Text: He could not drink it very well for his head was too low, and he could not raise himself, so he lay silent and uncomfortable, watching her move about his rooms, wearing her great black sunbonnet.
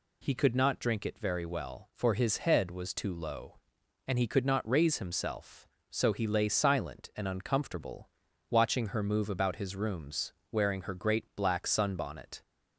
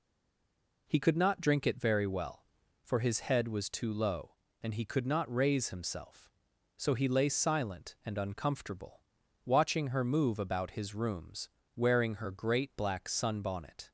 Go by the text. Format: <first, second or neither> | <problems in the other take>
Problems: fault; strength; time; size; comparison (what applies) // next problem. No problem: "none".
first | stays silent before the first word; slight; until 0.8 s; 0.8 s long